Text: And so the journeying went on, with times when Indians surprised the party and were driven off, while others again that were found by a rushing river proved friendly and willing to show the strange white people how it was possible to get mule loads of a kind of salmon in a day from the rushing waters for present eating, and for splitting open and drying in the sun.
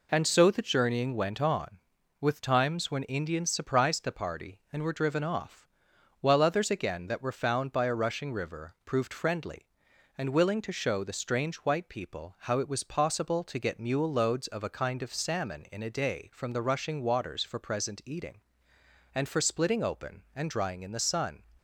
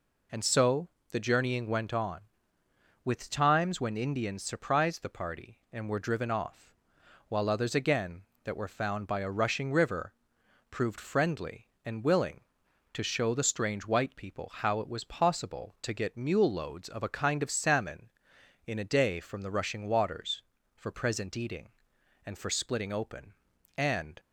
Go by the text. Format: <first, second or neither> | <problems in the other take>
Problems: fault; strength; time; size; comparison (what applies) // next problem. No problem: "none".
first | pauses between "so" and "the"; slight; at 0.8 s; 0.22 s long // pauses between "river" and "proved"; noticeable; at 10.1 s; 0.58 s long // stops before "drying in the sun"; at 24.1 s